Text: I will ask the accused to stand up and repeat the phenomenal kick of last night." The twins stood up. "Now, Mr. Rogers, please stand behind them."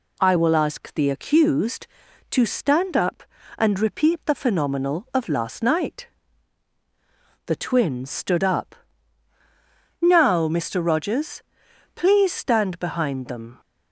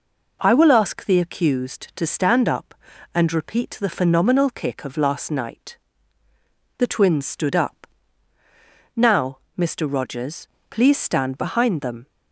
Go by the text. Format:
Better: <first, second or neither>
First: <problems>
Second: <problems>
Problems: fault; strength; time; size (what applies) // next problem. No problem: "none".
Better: second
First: skips "kick"; at 5.0 s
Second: none